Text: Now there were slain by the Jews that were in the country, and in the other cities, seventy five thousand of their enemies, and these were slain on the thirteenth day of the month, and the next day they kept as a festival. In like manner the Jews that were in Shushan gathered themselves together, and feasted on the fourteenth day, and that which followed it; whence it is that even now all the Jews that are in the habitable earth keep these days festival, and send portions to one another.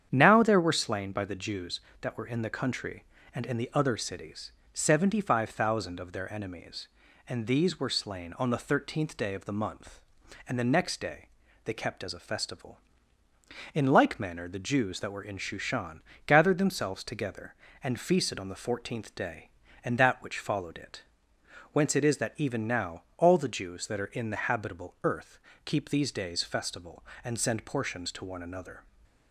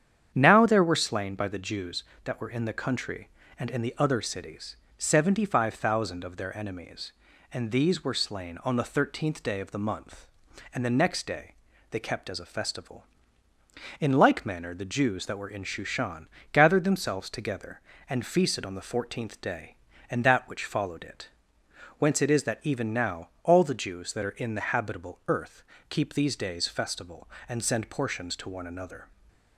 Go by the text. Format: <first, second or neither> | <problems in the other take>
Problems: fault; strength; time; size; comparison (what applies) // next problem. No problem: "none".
neither | starts louder than the rest; strong; the same in both // pauses between "day" and "they"; the same in both // pauses between "Shushan" and "gathered"; slight; the same in both // pauses between "now" and "all"; slight; the same in both // pauses between "earth" and "keep"; slight; the same in both